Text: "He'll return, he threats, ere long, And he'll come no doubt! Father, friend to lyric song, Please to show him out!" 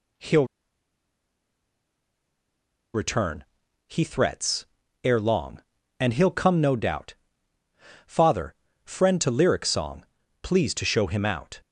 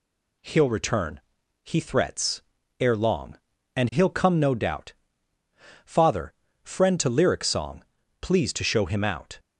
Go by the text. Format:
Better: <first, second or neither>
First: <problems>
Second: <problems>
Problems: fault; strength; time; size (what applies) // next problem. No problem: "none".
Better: second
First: pauses between "He'll" and "return"; strong; at 0.4 s; 2.4 s long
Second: none